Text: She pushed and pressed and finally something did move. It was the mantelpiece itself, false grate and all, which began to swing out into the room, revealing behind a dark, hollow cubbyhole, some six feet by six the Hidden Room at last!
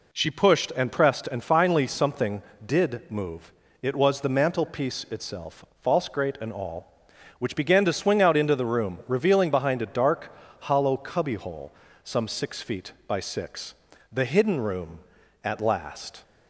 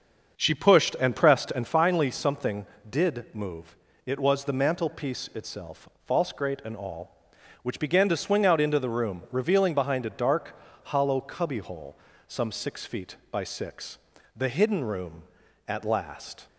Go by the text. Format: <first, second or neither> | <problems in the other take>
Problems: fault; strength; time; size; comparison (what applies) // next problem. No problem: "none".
first | starts louder than the rest; until 1.8 s; 6.5 dB // pauses between "six" and "the"; at 13.9 s; 0.40 s long; also in the first